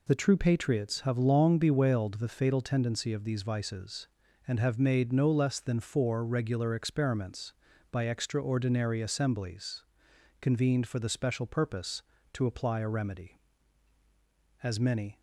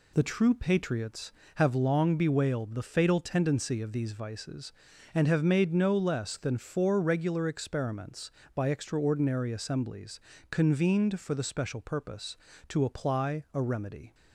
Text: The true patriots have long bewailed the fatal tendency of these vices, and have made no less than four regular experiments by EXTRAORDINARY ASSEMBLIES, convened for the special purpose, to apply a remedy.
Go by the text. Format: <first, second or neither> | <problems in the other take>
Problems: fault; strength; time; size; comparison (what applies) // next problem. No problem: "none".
second | goes on to say "As many"; from 14.6 s on; 0.56 s long